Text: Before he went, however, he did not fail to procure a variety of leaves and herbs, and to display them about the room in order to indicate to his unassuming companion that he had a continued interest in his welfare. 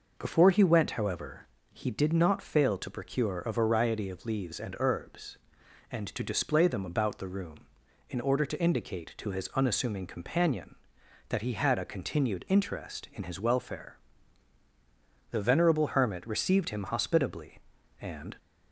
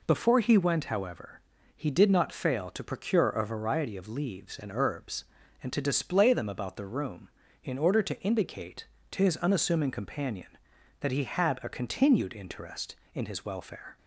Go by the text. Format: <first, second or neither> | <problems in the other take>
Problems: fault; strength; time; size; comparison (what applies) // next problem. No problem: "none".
second | goes on to say "The venerable hermit received him hospitably and"; strong; from 15.3 s on; 3.0 s long